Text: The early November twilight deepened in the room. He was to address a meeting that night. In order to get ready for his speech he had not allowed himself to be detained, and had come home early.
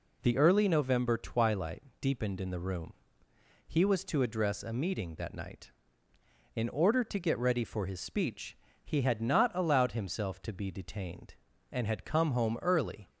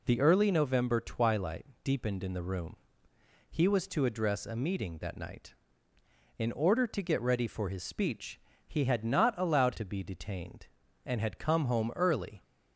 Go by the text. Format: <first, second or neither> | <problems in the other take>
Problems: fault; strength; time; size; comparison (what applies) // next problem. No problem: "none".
first | pauses between "twilight" and "deepened"; slight; at 1.6 s; 0.20 s long; slight in the first // pauses between "speech" and "he"; slight; at 8.3 s; 0.28 s long; slight in the first // skips "himself"; at 9.7 s